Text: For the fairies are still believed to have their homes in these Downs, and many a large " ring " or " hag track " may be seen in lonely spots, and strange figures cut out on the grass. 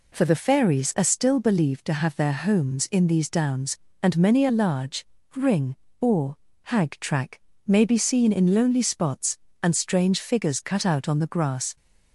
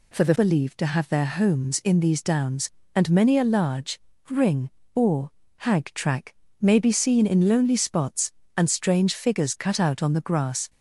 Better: first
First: none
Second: skips "fairies are still"; at 0.3 s

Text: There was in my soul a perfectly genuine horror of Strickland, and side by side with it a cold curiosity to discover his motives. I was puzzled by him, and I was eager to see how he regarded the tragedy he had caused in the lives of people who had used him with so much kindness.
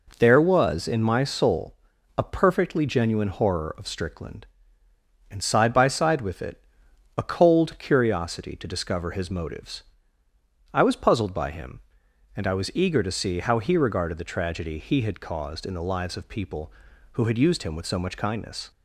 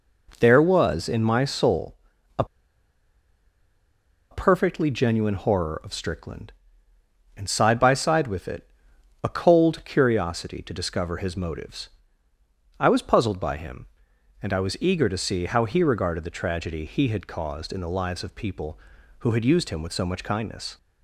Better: first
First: pauses between "soul" and "a"; at 1.7 s; 0.40 s long // pauses between "it" and "a"; noticeable; at 6.6 s; 0.56 s long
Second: pauses between "soul" and "a"; at 1.9 s; 0.40 s long // pauses between "a" and "perfectly"; strong; at 2.4 s; 1.8 s long // pauses between "it" and "a"; noticeable; at 8.6 s; 0.56 s long

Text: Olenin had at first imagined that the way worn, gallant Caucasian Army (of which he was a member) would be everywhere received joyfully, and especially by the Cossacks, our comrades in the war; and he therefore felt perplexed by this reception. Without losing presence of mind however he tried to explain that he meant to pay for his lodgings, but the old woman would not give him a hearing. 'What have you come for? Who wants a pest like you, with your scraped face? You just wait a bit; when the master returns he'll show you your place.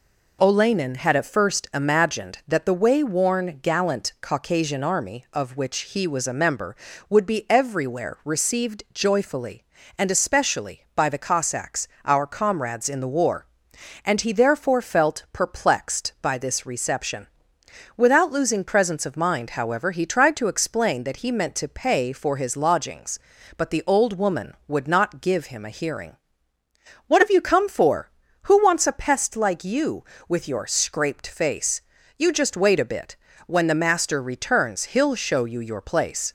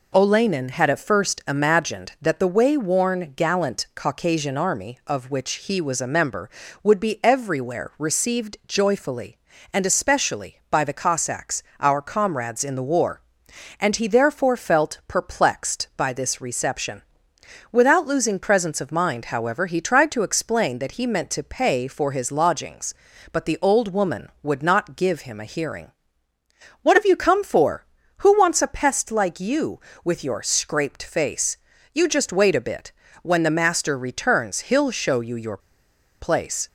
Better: first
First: none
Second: pauses between "your" and "place"; noticeable; at 35.5 s; 0.62 s long

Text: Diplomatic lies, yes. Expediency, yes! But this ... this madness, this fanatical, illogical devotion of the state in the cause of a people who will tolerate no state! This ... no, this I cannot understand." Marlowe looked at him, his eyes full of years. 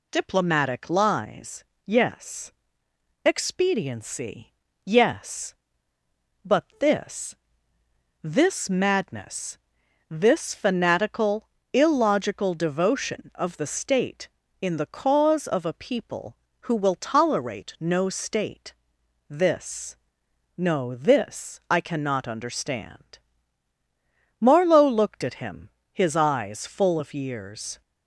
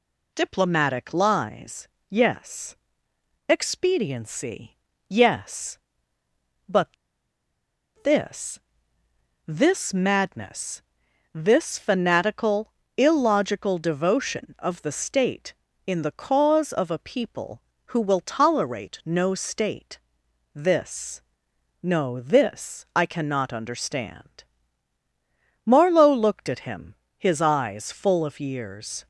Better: first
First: none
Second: pauses between "But" and "this"; at 6.8 s; 1.1 s long

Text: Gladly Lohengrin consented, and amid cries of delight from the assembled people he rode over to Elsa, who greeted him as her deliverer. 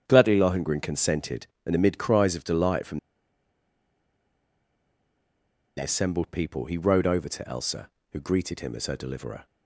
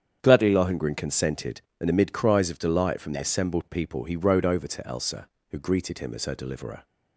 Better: second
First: starts louder than the rest; strong; until 1.0 s; 8.5 dB // pauses between "from" and "the"; strong; at 2.9 s; 2.7 s long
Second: starts louder than the rest; strong; until 1.2 s; 8.5 dB

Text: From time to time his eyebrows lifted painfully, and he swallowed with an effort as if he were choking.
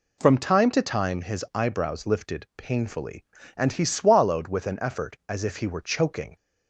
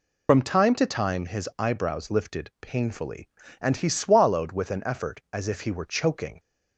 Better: first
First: none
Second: loses the start of "From"; at 0.2 s; 60 ms

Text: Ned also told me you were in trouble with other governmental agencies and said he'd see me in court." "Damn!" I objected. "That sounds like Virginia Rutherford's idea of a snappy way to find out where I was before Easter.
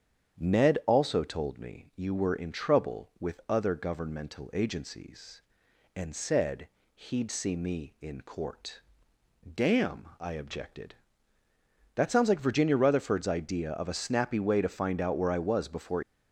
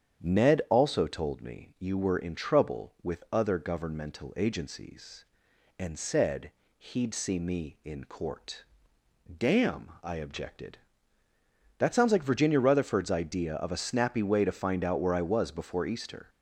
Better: second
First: starts louder than the rest; strong; until 1.4 s; 8.5 dB // pauses between "said" and "he'd"; slight; at 6.6 s; 0.26 s long // stops before "Easter"; at 16.0 s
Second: starts louder than the rest; strong; until 1.2 s; 8.5 dB // pauses between "said" and "he'd"; slight; at 6.5 s; 0.26 s long

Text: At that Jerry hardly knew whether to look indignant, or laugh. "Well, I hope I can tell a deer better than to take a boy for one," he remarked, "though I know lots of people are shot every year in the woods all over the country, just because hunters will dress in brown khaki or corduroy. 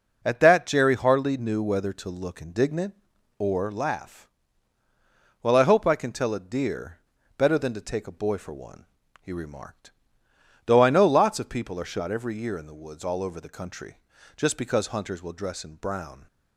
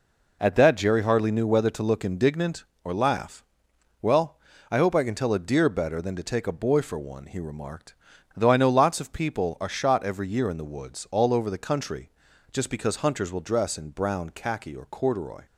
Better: second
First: pauses between "deer" and "better"; at 6.9 s; 0.38 s long // stops before "khaki or corduroy"; at 16.2 s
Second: none

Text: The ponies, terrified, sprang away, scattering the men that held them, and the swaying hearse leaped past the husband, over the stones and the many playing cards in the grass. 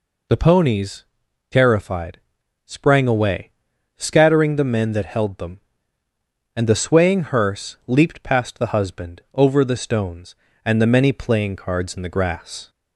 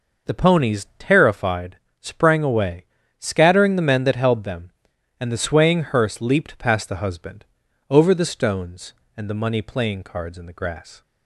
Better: first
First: none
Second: says "money" for "many"; at 9.4 s

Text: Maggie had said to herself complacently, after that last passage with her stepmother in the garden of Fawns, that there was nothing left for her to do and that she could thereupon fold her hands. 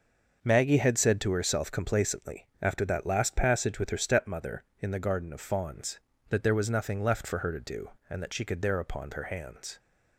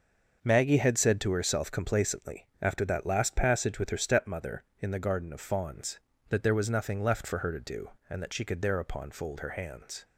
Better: second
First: starts louder than the rest; noticeable; until 1.4 s; 6 dB // skips "fold"; at 9.1 s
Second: starts louder than the rest; noticeable; until 1.4 s; 6 dB

